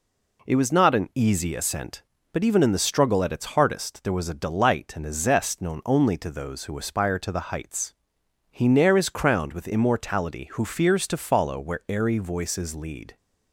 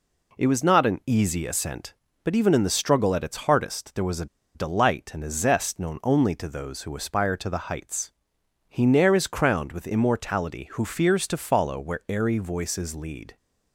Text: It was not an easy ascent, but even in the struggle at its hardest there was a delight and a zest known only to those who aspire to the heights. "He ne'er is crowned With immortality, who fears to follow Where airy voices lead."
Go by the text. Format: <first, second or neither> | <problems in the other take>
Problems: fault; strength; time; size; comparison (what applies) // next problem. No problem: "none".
first | pauses between "a" and "delight"; slight; at 4.2 s; 0.29 s long